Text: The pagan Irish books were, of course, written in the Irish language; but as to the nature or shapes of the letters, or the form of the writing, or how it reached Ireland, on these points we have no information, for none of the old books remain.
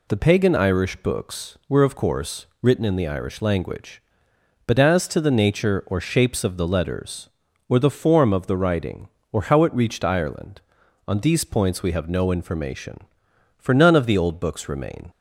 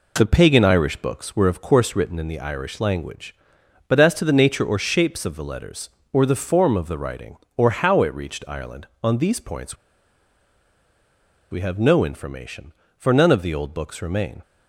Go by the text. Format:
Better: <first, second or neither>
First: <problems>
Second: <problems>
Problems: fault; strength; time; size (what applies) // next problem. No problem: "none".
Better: first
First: none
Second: pauses between "points" and "we"; strong; at 9.7 s; 1.7 s long